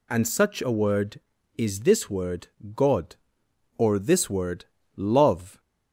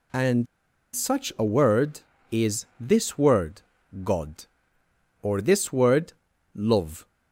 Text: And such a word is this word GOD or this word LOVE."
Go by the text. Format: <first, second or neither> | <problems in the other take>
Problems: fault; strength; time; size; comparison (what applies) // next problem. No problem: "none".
first | pauses between "And" and "such"; noticeable; at 0.4 s; 0.49 s long // pauses between "word" and "GOD"; at 3.6 s; 0.42 s long; slight in the first // pauses between "word" and "LOVE"; at 6.1 s; 0.42 s long; slight in the first